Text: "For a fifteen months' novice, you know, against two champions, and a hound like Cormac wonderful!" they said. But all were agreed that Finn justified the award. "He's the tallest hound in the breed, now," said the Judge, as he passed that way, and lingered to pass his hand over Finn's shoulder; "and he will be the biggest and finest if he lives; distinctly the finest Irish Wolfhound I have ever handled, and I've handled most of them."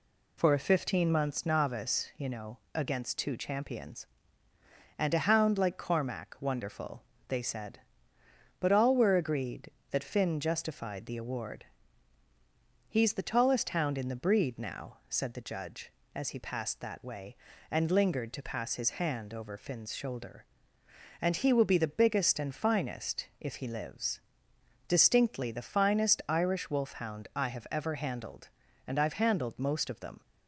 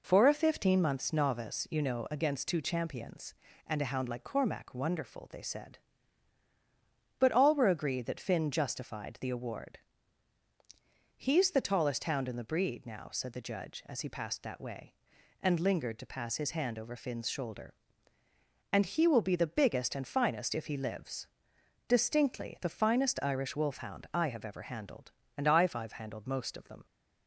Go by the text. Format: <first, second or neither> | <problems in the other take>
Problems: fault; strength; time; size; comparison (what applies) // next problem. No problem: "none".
first | says "I've" twice; at 25.7 s